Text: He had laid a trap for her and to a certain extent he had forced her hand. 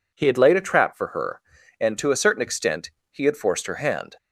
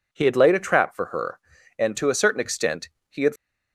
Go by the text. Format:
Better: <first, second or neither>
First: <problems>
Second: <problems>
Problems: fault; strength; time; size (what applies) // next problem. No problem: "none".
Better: first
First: pauses between "extent" and "he"; slight; at 2.9 s; 0.20 s long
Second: pauses between "extent" and "he"; slight; at 2.8 s; 0.20 s long // stops before "forced her hand"; at 3.3 s